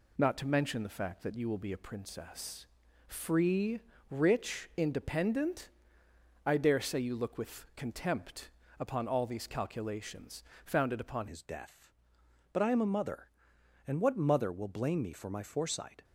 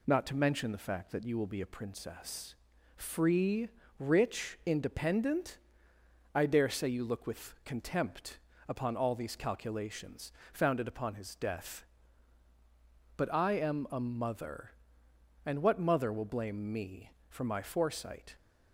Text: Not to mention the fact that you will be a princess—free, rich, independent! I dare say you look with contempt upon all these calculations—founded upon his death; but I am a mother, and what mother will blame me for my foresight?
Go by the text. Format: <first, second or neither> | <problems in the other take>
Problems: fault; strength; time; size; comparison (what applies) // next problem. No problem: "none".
second | pauses between "contempt" and "upon"; slight; at 8.4 s; 0.30 s long; slight in the second // changes voice at "his"; from 11.2 s on; 4.8 s long